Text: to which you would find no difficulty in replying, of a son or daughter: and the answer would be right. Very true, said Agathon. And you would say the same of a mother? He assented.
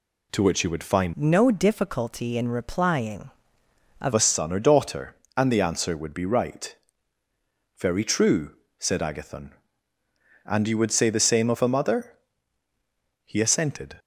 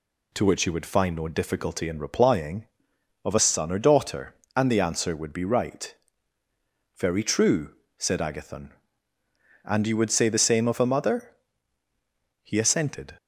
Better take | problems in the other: second | changes voice from "no" to "of"; from 1.1 to 4.1 s; 3.0 s long

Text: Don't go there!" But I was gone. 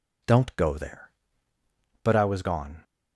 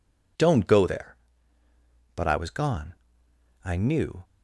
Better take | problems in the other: first | goes on to say "I knew"; from 3.6 s on; 0.60 s long

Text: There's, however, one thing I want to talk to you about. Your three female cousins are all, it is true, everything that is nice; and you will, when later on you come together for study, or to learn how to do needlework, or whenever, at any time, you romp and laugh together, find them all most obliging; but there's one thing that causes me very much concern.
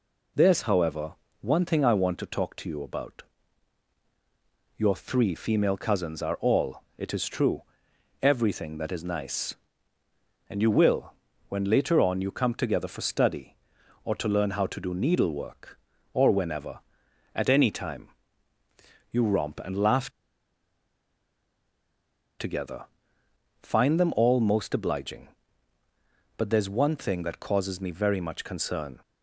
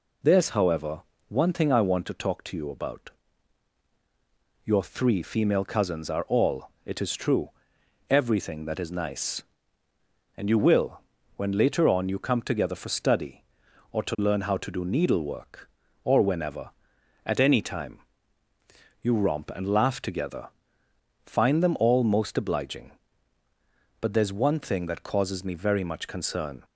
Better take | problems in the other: second | pauses between "laugh" and "together"; strong; at 20.0 s; 2.2 s long

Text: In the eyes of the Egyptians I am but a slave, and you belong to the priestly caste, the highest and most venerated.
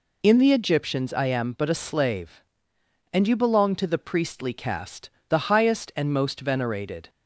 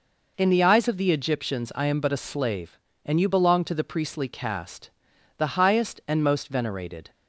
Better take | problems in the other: second | skips "eyes of the"; at 0.5 s

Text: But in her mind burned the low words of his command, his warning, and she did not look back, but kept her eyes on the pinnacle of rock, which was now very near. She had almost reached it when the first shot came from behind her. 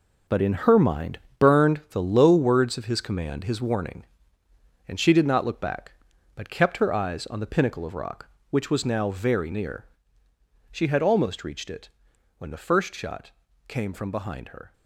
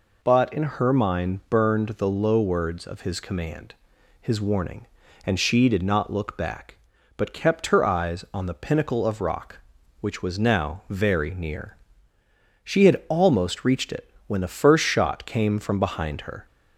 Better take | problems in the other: second | gets quieter; strong; throughout; 10.5 dB // pauses between "mind" and "burned"; slight; at 1.1 s; 0.20 s long // pauses between "it" and "when"; noticeable; at 11.8 s; 0.50 s long; slight in the second // pauses between "shot" and "came"; slight; at 13.3 s; 0.36 s long

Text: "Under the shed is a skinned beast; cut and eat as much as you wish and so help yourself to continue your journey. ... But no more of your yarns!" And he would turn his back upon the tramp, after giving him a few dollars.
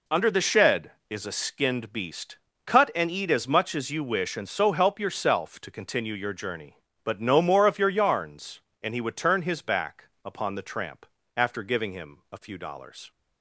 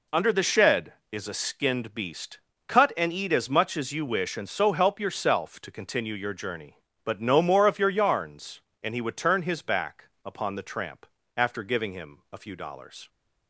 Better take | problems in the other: neither | pauses between "back" and "upon"; slight; the same in both

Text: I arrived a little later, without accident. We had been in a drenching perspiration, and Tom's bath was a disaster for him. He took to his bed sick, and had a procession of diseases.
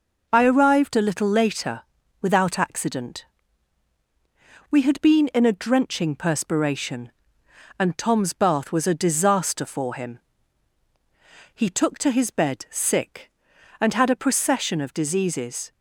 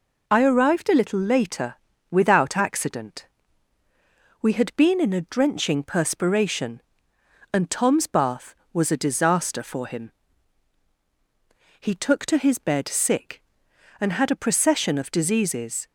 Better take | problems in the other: neither | none

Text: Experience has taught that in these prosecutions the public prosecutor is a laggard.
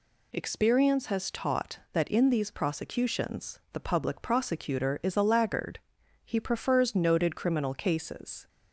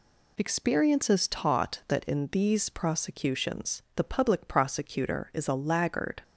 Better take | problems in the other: second | goes on to say "He prefers noted criminal cases"; strong; from 6.2 s on; 2.2 s long

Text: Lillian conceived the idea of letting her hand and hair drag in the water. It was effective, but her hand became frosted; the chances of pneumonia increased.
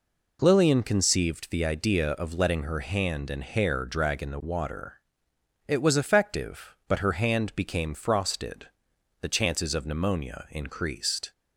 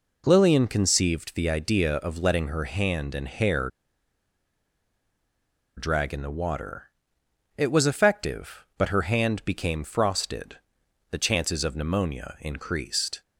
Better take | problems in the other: first | pauses between "hair" and "drag"; strong; at 3.6 s; 2.0 s long

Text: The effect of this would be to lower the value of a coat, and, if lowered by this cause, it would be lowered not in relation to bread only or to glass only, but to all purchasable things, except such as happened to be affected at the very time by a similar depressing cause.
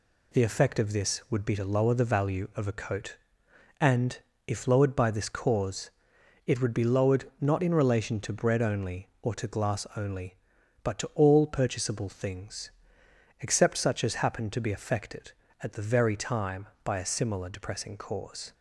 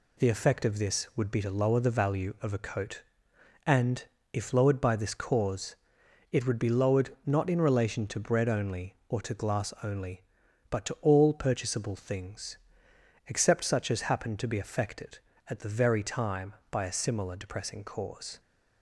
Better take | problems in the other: neither | none

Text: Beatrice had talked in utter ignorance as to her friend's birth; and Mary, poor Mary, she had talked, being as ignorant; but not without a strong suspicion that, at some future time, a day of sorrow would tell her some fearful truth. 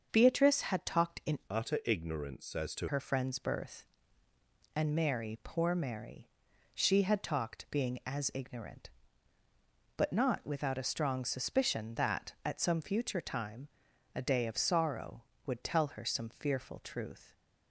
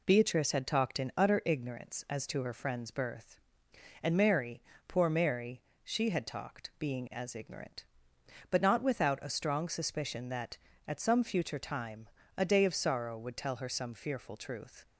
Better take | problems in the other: second | starts louder than the rest; until 1.1 s; 6.5 dB // changes voice from "utter" to "to"; from 1.4 to 2.8 s; 1.4 s long

